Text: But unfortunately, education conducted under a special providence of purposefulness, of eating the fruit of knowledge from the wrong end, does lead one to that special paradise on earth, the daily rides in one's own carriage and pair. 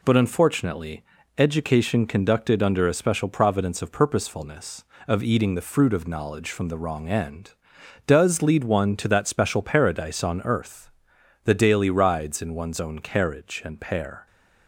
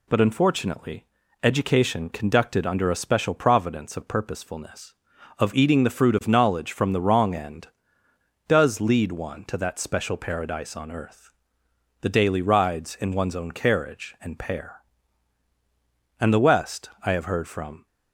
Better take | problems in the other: first | goes on to say "And the West I have heard from"; from 16.1 s on; 1.6 s long

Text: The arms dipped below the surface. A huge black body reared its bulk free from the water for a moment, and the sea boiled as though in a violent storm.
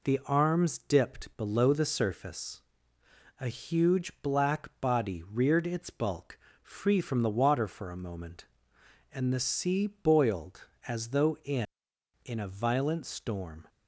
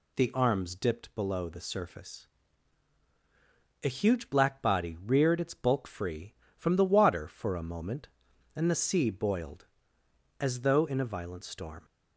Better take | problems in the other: second | pauses between "bulk" and "free"; slight; at 6.3 s; 0.22 s long // says "in" twice; at 12.2 s

